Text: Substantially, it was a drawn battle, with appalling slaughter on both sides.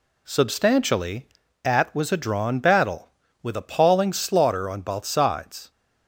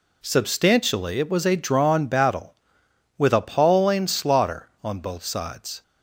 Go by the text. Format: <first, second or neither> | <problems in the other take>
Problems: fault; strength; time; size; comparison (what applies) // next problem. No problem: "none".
second | says "at" for "it"; at 1.6 s